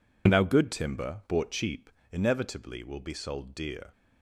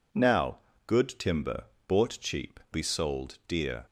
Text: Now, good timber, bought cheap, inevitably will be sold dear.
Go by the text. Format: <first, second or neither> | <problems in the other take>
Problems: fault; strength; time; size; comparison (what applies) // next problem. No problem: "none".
first | skips "inevitably will"; at 2.6 s